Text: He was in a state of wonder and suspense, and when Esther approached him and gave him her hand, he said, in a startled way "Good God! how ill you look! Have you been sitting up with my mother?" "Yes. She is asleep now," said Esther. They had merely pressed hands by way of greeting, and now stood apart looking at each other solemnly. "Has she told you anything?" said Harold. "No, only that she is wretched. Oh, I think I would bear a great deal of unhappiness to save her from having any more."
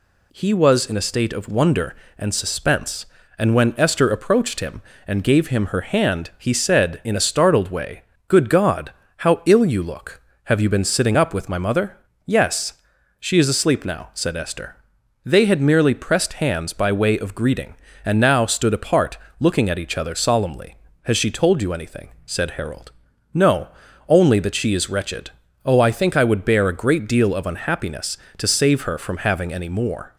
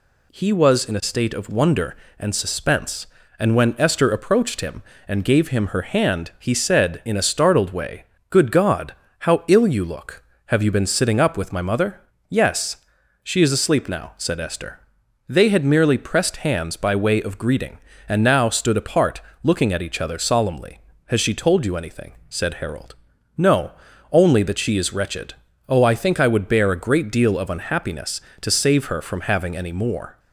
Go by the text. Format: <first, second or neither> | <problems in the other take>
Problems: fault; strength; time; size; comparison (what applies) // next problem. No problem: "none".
neither | pauses between "way" and "Good"; slight; the same in both // pauses between "apart" and "looking"; slight; the same in both